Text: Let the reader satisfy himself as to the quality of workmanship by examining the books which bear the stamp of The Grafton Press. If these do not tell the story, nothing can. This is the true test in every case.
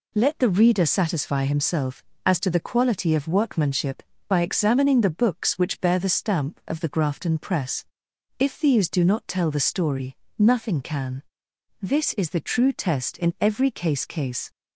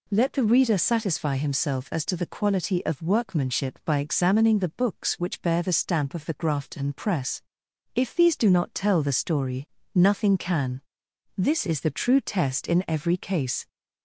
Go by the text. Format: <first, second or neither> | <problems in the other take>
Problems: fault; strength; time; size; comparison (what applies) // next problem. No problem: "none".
second | says "case" twice; at 14.0 s